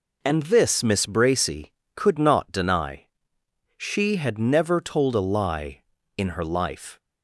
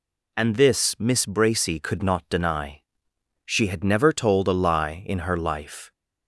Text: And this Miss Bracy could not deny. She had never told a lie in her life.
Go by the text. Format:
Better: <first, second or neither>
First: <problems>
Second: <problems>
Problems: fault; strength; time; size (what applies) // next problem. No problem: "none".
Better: neither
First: none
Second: none